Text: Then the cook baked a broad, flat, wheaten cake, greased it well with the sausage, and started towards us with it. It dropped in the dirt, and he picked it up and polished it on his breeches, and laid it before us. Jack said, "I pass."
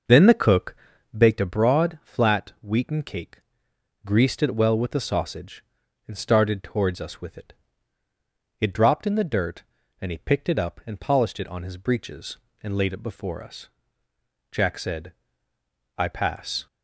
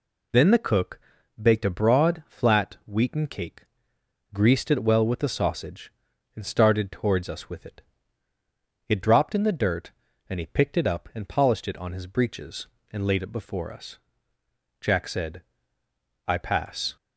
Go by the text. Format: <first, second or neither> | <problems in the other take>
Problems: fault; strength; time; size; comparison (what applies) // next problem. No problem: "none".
second | starts louder than the rest; noticeable; until 1.4 s; 6 dB // pauses between "cook" and "baked"; at 0.7 s; 0.40 s long; also in the second